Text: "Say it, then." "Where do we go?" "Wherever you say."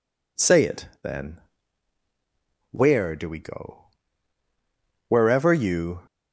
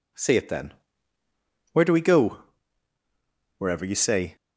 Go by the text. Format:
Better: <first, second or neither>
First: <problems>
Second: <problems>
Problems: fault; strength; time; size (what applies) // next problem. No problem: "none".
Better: second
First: stops before "say"; at 6.0 s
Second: none